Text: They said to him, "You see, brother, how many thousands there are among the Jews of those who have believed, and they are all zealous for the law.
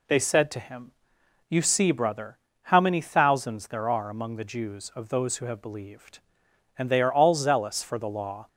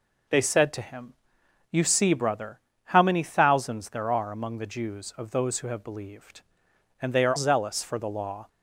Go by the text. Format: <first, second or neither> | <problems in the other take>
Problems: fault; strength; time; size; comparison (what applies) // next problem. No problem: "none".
first | skips "all"; at 7.3 s